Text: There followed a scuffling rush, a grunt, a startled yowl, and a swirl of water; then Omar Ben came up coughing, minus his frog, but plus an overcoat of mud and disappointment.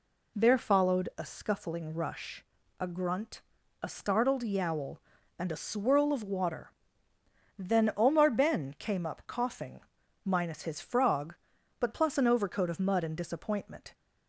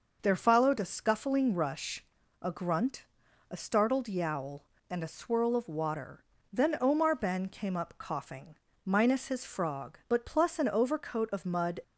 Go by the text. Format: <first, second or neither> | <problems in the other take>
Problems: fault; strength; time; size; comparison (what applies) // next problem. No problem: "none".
first | stops before "and disappointment"; at 11.8 s